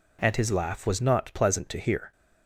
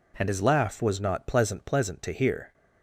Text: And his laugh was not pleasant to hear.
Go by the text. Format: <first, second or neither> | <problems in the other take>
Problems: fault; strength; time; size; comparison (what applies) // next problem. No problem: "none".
first | says "pleasant" twice; at 1.6 s